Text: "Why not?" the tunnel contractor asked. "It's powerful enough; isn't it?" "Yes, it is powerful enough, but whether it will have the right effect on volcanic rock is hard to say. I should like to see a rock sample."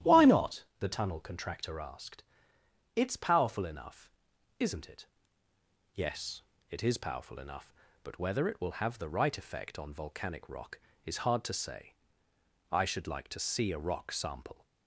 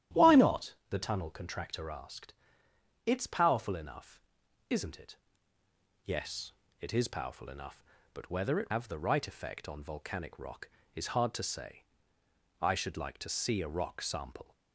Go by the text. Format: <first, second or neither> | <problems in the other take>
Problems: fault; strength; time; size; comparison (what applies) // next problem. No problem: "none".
first | starts louder than the rest; strong; until 1.3 s; 11.5 dB; strong in the first // skips "will"; at 8.7 s